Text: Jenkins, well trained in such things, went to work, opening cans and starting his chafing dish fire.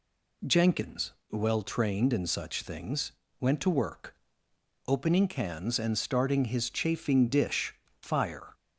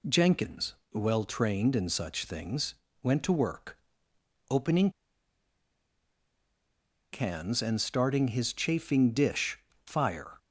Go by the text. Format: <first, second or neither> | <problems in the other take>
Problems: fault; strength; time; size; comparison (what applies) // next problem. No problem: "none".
first | pauses between "opening" and "cans"; strong; at 4.8 s; 2.2 s long // pauses between "dish" and "fire"; slight; at 9.5 s; 0.30 s long; slight in the first